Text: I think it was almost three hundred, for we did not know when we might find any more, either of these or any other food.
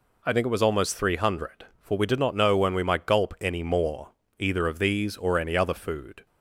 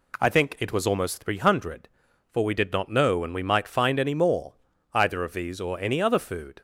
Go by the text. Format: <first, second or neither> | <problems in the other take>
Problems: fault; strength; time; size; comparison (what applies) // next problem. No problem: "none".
second | says "gulp" for "find"; at 3.0 s